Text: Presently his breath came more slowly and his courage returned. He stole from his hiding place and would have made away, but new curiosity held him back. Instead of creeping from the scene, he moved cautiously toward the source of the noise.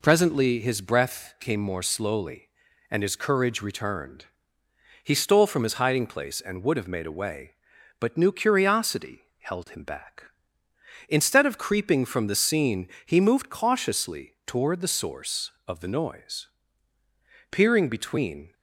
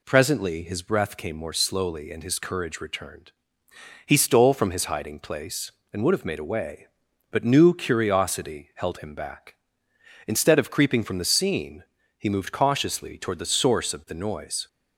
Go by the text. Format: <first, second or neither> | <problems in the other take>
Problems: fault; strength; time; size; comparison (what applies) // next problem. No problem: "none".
second | pauses between "curiosity" and "held"; slight; at 9.2 s; 0.18 s long // goes on to say "Peering between"; noticeable; from 17.4 s on; 1.0 s long